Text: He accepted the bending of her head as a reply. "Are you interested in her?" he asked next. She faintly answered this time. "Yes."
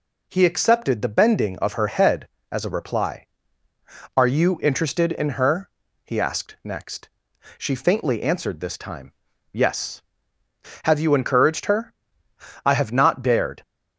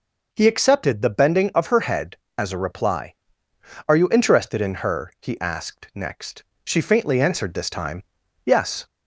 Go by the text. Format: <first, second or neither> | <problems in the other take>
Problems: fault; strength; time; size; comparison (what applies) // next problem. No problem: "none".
second | goes on to say "Have you encouraged her I have not dared"; strong; from 10.8 s on; 2.7 s long